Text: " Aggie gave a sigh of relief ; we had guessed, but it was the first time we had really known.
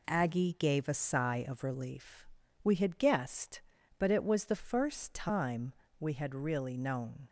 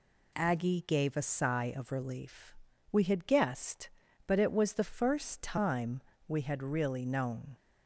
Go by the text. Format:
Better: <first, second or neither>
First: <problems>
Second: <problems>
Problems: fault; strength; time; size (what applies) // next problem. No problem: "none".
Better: second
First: gets quieter; noticeable; throughout; 5 dB // pauses between "time" and "we"; slight; at 5.7 s; 0.26 s long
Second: pauses between "time" and "we"; slight; at 6.0 s; 0.26 s long